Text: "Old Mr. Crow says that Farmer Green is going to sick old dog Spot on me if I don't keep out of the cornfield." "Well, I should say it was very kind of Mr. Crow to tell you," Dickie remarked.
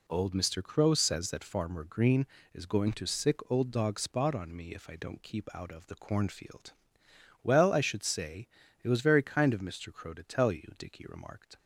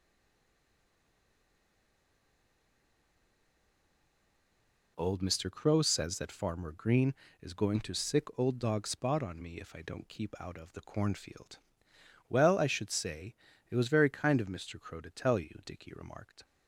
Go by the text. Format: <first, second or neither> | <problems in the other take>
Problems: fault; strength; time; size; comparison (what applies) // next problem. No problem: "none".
first | stays silent before the first word; strong; until 4.9 s; 4.9 s long // pauses between "say" and "it"; slight; at 13.3 s; 0.36 s long; slight in the first